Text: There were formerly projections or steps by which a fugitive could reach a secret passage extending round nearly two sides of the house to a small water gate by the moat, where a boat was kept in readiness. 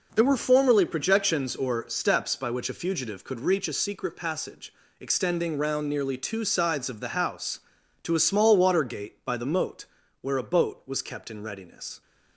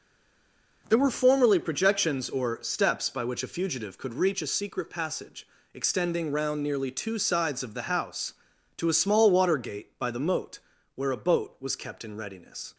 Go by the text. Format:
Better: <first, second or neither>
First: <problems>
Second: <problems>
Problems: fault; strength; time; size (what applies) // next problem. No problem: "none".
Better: first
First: pauses between "passage" and "extending"; slight; at 4.7 s; 0.26 s long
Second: stays silent before the first word; slight; until 0.8 s; 0.8 s long // pauses between "passage" and "extending"; slight; at 5.4 s; 0.26 s long